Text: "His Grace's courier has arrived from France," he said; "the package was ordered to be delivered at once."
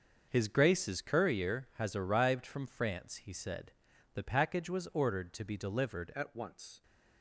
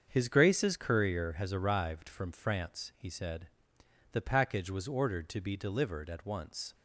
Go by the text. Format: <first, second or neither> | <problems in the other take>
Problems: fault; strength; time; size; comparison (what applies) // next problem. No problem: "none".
second | starts louder than the rest; until 1.3 s; 6.5 dB; strong in the second // changes voice at "at"; from 6.1 s on; 0.7 s long